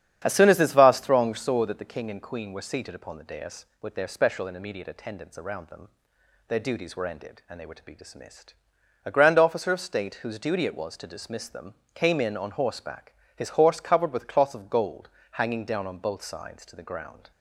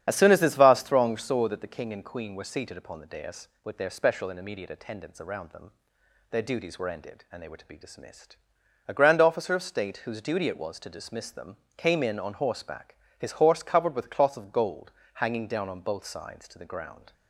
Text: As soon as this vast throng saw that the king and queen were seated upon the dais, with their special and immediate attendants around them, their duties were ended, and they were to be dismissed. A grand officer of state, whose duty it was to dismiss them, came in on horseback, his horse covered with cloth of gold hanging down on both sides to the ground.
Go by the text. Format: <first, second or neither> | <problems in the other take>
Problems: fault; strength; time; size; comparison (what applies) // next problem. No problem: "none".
first | loses the start of "As"; at 0.0 s; 30 ms // starts louder than the rest; strong; until 1.0 s; 9 dB; strong in the first // pauses between "gold" and "hanging"; slight; at 14.9 s; 0.22 s long; slight in the first